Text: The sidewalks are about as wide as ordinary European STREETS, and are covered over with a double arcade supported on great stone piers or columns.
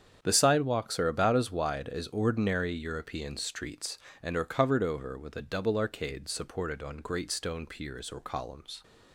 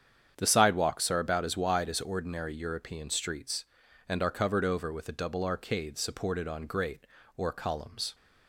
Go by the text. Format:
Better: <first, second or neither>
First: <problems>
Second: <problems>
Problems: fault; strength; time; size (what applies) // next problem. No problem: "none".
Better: first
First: starts louder than the rest; strong; until 1.2 s; 8 dB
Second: starts louder than the rest; strong; until 1.3 s; 8.5 dB // skips "stone piers"; at 7.2 s